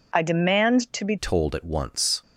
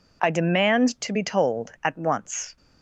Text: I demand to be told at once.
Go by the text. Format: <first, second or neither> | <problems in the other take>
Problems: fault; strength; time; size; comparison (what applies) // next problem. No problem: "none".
second | changes voice at "told"; from 1.1 s on; 1.1 s long